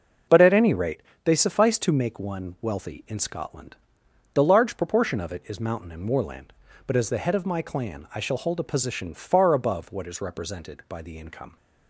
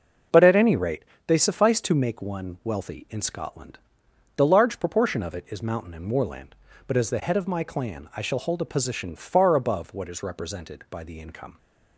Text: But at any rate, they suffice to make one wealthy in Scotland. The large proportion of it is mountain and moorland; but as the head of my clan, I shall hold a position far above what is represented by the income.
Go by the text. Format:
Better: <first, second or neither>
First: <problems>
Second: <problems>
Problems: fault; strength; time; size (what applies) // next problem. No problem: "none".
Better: neither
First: none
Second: none